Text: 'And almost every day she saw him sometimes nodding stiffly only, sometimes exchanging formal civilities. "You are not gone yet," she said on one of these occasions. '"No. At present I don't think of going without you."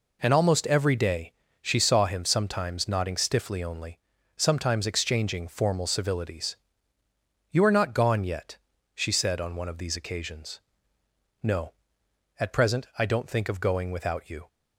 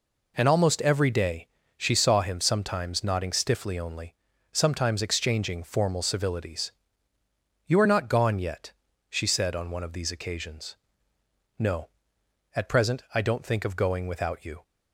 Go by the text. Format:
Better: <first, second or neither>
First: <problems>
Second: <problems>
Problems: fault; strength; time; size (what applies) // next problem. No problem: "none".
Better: neither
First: pauses between "day" and "she"; slight; at 1.3 s; 0.27 s long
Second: pauses between "day" and "she"; slight; at 1.4 s; 0.28 s long